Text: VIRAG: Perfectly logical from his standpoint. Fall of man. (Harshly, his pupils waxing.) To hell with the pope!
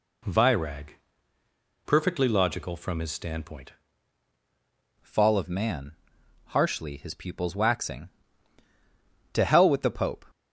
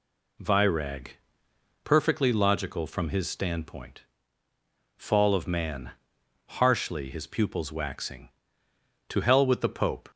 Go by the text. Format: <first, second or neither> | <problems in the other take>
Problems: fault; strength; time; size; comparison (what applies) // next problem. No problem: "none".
second | changes voice at "Fall"; from 5.0 s on; 5.2 s long